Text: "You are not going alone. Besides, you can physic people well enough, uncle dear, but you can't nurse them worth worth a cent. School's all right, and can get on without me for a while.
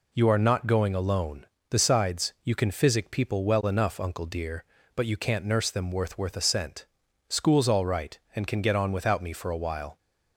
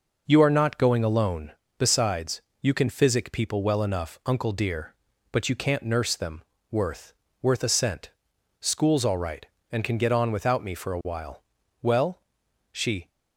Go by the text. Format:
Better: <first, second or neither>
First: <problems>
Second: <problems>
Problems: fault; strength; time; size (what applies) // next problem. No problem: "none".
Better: first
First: none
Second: pauses between "them" and "worth"; slight; at 6.4 s; 0.30 s long // pauses between "worth" and "worth"; slight; at 7.1 s; 0.30 s long // goes on to say "Well She"; noticeable; from 11.8 s on; 1.2 s long